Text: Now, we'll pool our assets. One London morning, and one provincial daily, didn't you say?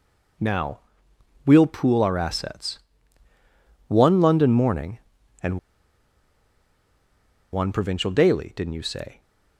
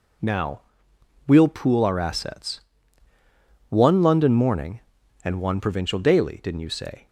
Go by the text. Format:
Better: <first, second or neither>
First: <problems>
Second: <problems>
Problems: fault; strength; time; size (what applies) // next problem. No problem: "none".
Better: second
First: pauses between "and" and "one"; strong; at 5.5 s; 1.9 s long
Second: none